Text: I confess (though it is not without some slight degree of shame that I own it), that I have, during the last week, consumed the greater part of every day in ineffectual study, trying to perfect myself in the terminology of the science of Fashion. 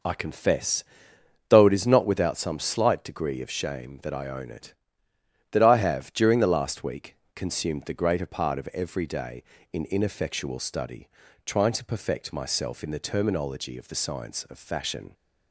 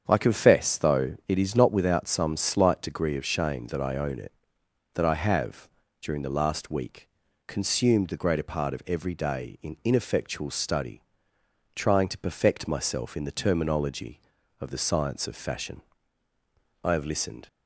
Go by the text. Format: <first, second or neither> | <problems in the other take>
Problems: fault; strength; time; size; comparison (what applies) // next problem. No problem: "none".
first | starts louder than the rest; strong; until 1.0 s; 7.5 dB // goes on to say "I have listened"; noticeable; from 16.8 s on; 0.64 s long